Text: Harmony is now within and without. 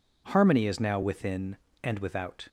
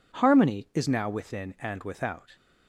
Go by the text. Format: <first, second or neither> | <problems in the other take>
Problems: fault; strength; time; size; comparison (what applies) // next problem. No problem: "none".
neither | none